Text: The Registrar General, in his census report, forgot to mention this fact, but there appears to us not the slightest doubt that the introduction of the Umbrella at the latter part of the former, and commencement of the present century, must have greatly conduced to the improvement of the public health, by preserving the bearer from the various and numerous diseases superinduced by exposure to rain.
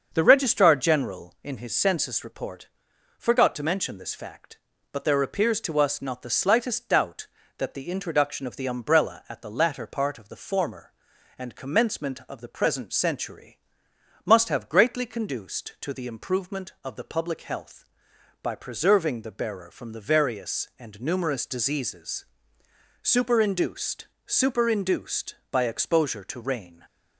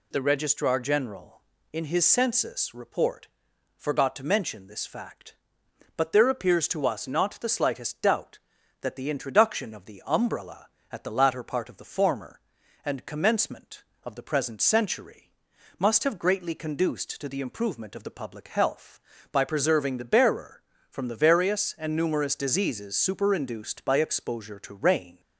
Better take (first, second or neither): second